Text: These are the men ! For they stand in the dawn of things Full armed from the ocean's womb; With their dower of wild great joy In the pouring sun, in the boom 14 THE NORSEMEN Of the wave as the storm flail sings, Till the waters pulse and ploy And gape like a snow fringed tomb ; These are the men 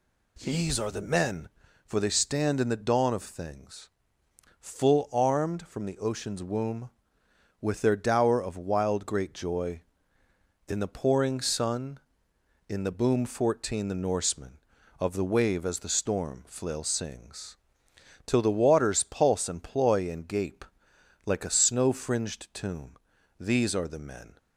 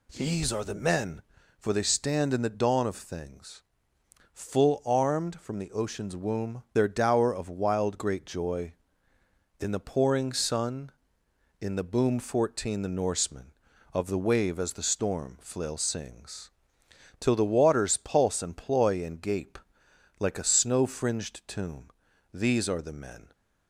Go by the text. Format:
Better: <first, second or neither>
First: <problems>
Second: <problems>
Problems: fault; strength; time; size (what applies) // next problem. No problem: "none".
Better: first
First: pauses between "things" and "Full"; noticeable; at 3.8 s; 0.70 s long // pauses between "gape" and "like"; noticeable; at 20.6 s; 0.62 s long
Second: pauses between "things" and "Full"; noticeable; at 3.6 s; 0.70 s long // skips "With"; at 6.6 s // pauses between "gape" and "like"; noticeable; at 19.5 s; 0.62 s long